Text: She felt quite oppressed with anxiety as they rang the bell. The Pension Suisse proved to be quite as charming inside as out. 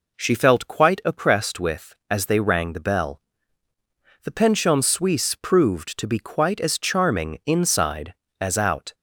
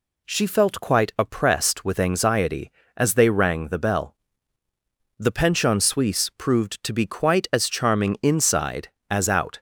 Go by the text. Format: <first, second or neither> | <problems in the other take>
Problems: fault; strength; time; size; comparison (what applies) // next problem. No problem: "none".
second | skips "anxiety"; at 2.0 s